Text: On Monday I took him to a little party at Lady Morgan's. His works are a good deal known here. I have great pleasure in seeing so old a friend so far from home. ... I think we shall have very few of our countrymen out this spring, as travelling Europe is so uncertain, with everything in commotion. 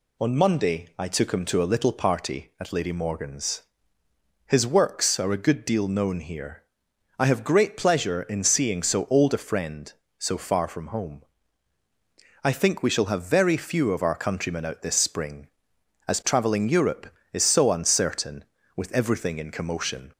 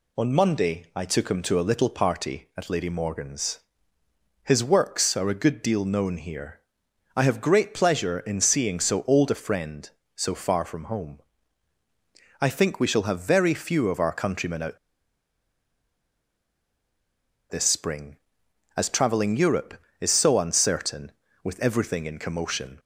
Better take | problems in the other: first | pauses between "out" and "this"; strong; at 14.7 s; 2.7 s long

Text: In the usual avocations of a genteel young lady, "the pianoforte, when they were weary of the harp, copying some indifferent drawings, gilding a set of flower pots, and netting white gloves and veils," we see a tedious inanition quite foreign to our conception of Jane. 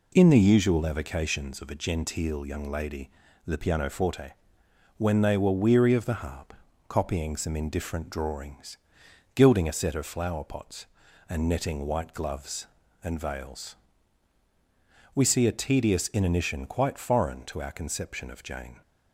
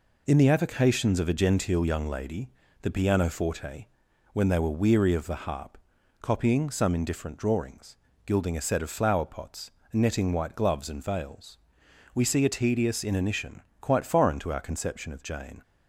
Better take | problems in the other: first | skips "usual"; at 0.4 s // pauses between "inanition" and "quite"; slight; at 13.6 s; 0.22 s long

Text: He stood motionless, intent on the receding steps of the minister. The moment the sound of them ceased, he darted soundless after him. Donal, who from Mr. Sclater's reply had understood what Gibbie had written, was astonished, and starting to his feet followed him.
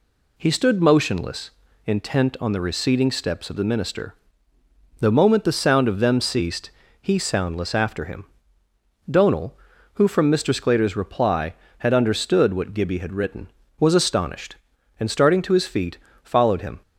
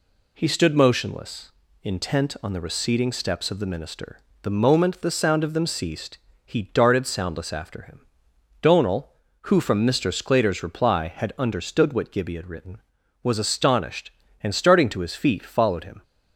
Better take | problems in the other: second | skips "darted"; at 7.1 s // pauses between "feet" and "followed"; slight; at 15.9 s; 0.26 s long

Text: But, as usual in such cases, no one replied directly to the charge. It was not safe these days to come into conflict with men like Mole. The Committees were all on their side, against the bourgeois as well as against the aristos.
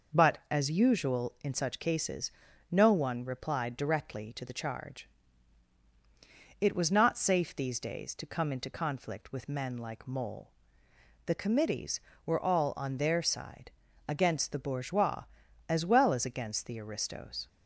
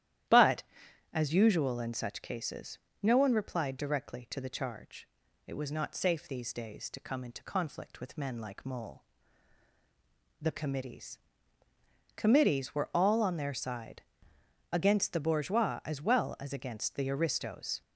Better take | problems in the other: first | starts louder than the rest; strong; until 1.7 s; 12 dB // says "Committees" twice; at 12.1 s

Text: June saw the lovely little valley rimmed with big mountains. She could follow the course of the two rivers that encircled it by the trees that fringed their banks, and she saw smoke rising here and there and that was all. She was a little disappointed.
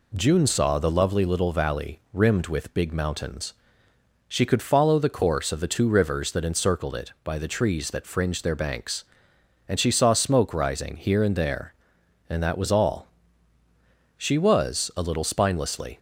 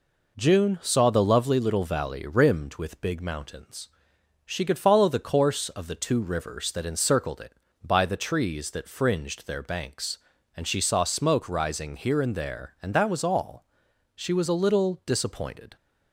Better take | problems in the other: second | says "spinelessly" for "disappointed"; at 15.2 s

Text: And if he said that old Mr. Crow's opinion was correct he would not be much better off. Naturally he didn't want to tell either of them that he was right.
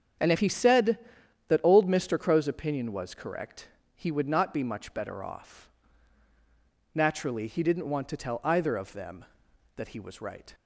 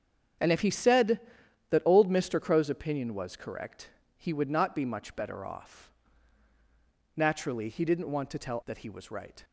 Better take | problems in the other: first | starts louder than the rest; strong; until 1.9 s; 8 dB; strong in the first // pauses between "correct" and "he"; slight; at 3.9 s; 0.30 s long; slight in the first // skips "either of them"; at 8.6 s

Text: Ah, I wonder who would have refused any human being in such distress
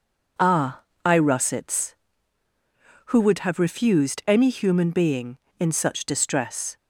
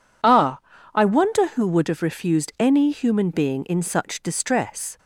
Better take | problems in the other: second | says "russets" for "wonder"; at 1.1 s

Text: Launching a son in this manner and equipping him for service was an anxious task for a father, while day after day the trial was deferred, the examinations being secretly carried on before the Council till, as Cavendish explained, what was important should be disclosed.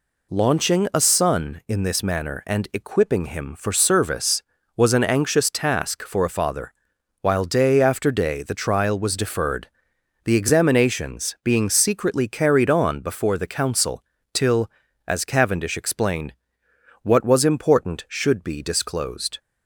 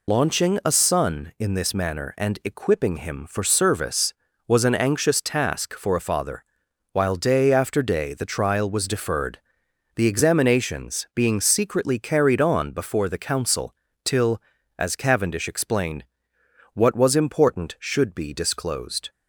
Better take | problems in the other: first | loses the start of "Launching"; at 0.0 s; 60 ms // pauses between "Council" and "till"; slight; at 13.7 s; 0.30 s long; slight in the first

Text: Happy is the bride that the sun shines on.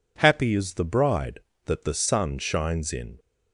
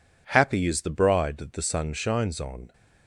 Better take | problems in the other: second | says "in" for "on"; at 2.9 s

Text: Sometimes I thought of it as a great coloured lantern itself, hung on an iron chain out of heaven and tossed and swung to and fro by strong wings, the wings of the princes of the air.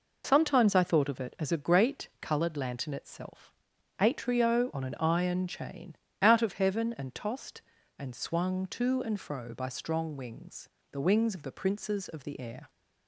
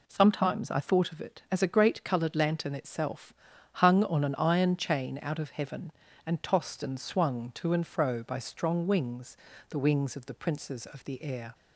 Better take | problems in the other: second | says "atrio" for "hung"; at 3.9 s // pauses between "chain" and "out"; slight; at 5.9 s; 0.24 s long

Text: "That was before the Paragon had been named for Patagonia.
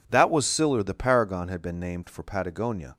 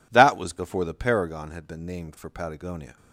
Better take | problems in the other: second | says "siller" for "before"; at 0.4 s

